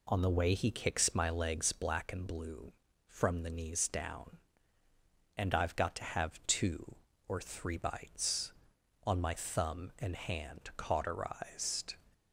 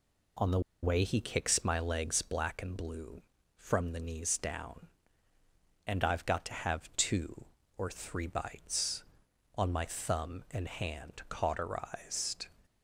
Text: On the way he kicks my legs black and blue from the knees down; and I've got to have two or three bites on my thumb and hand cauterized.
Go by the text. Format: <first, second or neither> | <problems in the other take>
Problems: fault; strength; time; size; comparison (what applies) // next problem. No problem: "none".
first | pauses between "the" and "way"; slight; at 0.5 s; 0.23 s long